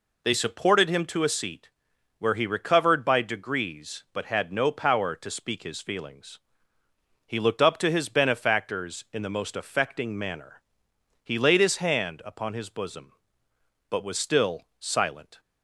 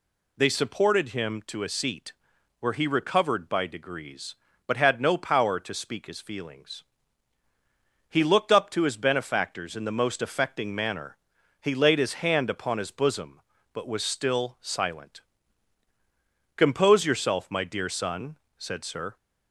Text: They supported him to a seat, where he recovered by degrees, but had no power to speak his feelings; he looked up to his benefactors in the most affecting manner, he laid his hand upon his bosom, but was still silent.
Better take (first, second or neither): first